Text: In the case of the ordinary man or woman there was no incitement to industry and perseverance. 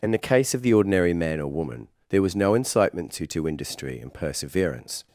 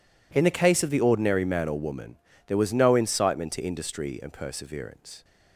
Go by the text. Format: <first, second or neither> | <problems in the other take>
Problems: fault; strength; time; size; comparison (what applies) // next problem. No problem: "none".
second | pauses between "woman" and "there"; slight; at 1.8 s; 0.22 s long; slight in the second // says "to" twice; at 3.2 s